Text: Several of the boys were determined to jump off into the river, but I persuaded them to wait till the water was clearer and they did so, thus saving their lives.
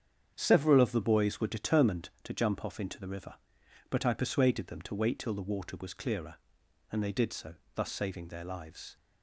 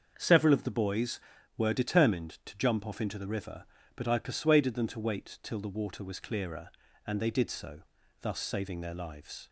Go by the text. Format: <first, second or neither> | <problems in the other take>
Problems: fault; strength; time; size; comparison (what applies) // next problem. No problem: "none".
neither | starts louder than the rest; the same in both